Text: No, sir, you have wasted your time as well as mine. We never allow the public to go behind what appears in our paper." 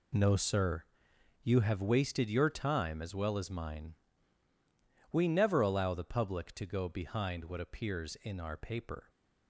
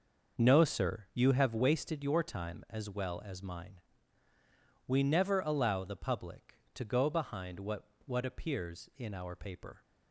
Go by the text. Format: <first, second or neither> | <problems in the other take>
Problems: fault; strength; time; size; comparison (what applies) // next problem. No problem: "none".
first | starts louder than the rest; noticeable; until 1.4 s; 6 dB // says "what" twice; at 8.0 s